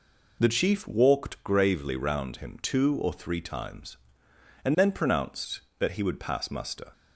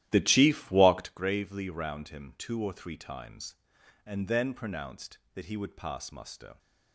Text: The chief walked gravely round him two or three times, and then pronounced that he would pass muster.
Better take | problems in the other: first | starts louder than the rest; strong; until 1.1 s; 13 dB

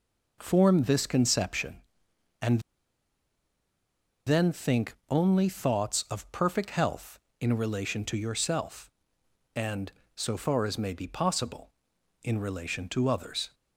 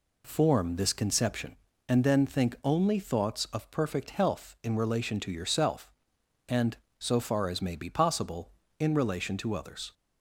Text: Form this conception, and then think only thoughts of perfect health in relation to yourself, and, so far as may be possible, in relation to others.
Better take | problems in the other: second | pauses between "and" and "then"; strong; at 2.6 s; 1.6 s long // pauses between "think" and "only"; slight; at 4.9 s; 0.16 s long

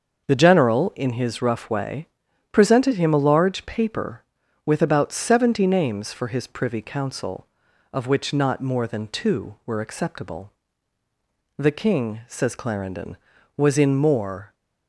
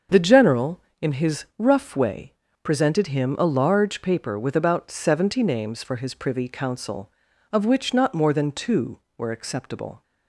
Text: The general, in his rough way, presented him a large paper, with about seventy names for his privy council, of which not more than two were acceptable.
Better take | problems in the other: second | starts louder than the rest; until 1.3 s; 6.5 dB; also in the second // goes on to say "The king says Clarendon was in more"; strong; from 11.5 s on; 2.9 s long

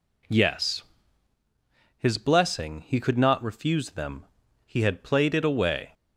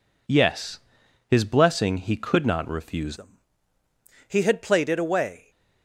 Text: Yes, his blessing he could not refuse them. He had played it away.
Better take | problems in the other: first | changes voice at "them"; from 3.1 s on; 2.4 s long

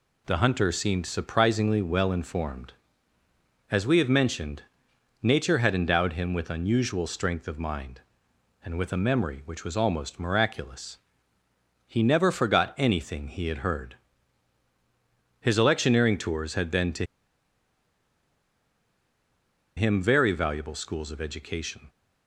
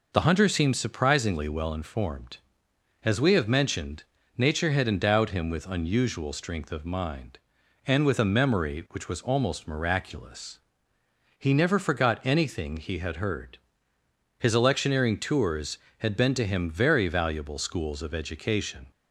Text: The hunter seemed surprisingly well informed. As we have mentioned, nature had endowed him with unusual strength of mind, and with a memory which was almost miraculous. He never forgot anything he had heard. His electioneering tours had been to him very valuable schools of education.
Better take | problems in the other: second | pauses between "to" and "him"; strong; at 17.0 s; 2.7 s long

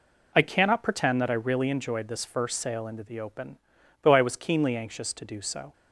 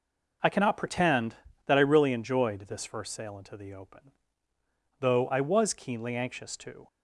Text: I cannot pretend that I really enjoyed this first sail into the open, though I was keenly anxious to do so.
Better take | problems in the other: first | stops before "do so"; at 6.8 s

